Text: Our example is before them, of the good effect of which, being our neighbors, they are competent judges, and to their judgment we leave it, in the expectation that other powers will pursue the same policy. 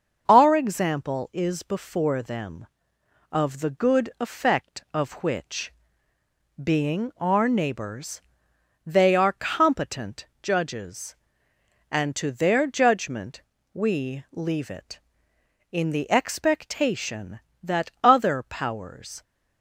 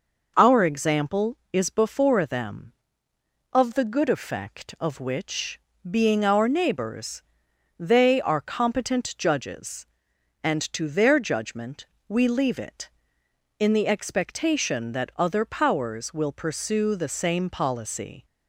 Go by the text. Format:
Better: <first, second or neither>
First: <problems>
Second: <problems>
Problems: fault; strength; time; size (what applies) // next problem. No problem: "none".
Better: second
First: starts louder than the rest; until 1.2 s; 6.5 dB // pauses between "competent" and "judges"; slight; at 10.2 s; 0.16 s long // pauses between "judgment" and "we"; slight; at 13.4 s; 0.30 s long // stops before "will pursue the same policy"; at 19.2 s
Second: pauses between "judgment" and "we"; slight; at 11.8 s; 0.23 s long